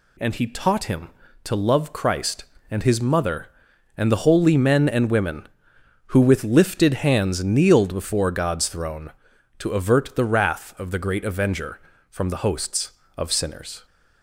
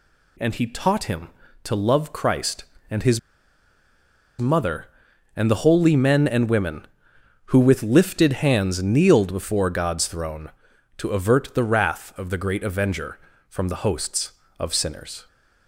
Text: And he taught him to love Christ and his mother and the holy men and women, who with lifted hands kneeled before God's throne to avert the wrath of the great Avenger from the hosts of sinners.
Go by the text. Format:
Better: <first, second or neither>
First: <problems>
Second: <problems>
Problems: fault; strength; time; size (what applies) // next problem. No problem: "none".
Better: first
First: none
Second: pauses between "his" and "mother"; at 3.1 s; 1.1 s long